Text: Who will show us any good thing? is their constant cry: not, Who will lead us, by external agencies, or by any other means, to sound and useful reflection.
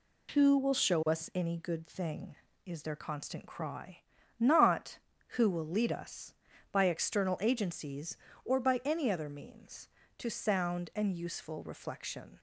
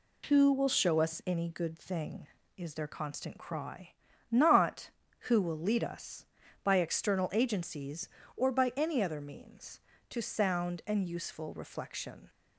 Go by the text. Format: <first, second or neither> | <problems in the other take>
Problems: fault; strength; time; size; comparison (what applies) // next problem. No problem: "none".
neither | none